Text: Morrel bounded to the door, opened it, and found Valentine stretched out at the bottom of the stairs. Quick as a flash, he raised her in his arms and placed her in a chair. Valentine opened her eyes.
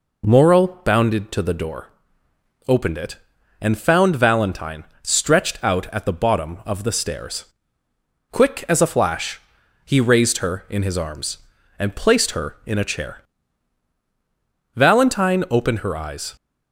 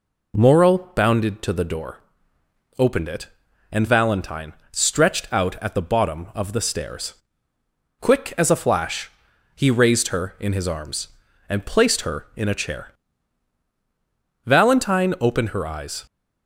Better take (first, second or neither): first